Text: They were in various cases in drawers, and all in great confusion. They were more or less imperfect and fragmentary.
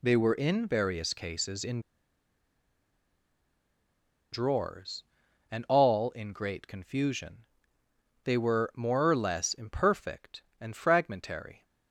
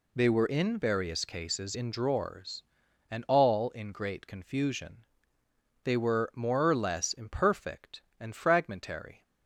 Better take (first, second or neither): second